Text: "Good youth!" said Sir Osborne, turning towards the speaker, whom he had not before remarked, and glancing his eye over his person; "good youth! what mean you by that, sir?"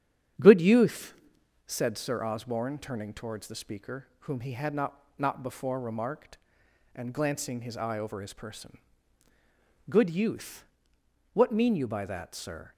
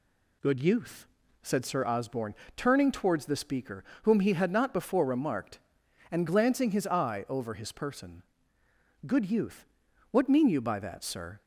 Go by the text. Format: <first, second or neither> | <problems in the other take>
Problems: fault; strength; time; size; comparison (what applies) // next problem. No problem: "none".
second | starts louder than the rest; strong; until 1.9 s; 9 dB // says "not" twice; at 5.1 s